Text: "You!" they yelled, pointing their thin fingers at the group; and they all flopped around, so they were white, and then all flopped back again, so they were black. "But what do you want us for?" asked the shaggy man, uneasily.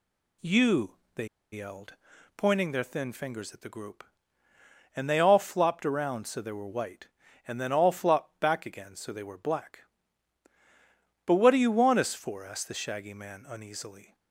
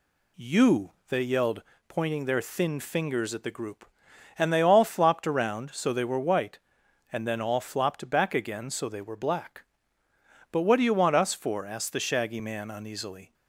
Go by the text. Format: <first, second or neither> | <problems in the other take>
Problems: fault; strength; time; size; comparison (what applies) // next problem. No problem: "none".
second | pauses between "they" and "yelled"; slight; at 1.2 s; 0.25 s long